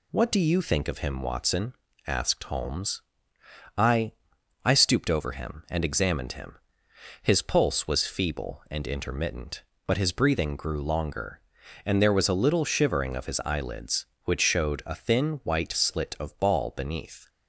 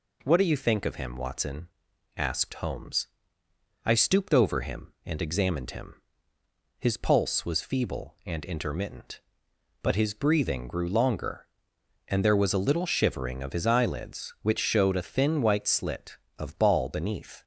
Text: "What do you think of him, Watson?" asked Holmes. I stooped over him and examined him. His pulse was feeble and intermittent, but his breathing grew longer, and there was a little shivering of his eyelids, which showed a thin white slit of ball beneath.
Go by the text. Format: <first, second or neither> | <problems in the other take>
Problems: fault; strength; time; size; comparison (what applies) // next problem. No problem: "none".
second | says "I" twice; at 4.6 s